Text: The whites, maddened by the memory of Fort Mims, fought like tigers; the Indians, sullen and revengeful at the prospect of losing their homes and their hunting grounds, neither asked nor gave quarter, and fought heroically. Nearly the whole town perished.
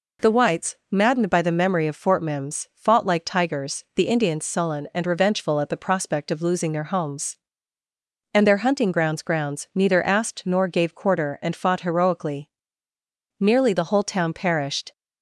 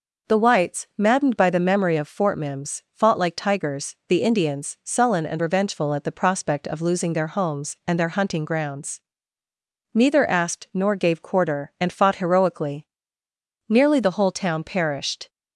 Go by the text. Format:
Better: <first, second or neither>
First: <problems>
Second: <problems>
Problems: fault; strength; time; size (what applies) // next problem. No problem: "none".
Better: second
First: says "grounds" twice; at 9.2 s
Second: none